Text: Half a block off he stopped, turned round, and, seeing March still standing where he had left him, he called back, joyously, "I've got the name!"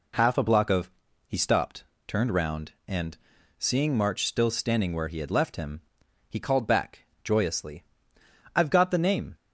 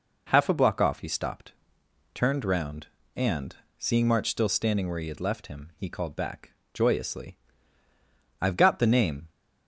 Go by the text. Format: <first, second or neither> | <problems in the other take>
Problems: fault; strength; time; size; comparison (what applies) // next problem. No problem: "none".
second | says "of" for "off"; at 0.7 s